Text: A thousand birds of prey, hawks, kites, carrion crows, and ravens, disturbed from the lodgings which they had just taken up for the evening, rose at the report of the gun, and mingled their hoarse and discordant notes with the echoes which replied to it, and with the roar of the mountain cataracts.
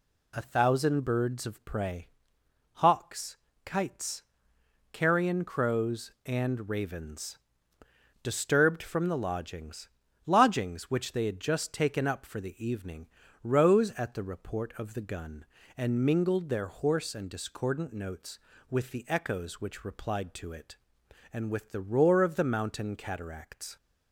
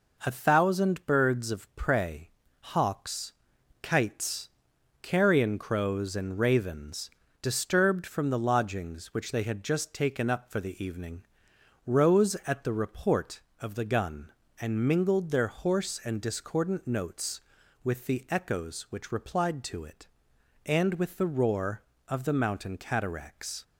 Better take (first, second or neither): second